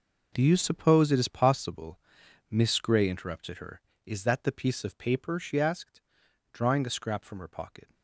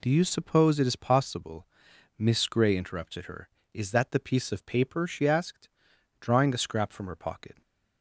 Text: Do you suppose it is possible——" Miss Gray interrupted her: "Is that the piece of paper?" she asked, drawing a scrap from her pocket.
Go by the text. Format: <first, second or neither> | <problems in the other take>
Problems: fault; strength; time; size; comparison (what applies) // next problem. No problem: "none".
second | gets quieter; strong; throughout; 14 dB